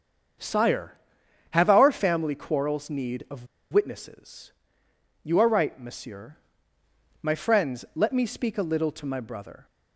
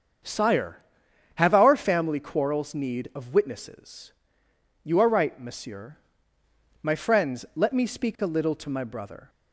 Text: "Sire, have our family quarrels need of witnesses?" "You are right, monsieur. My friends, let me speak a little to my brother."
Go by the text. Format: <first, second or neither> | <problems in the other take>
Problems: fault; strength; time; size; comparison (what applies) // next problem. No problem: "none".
second | starts louder than the rest; strong; until 1.9 s; 7.5 dB; strong in the second // pauses between "of" and "witnesses"; slight; at 3.4 s; 0.26 s long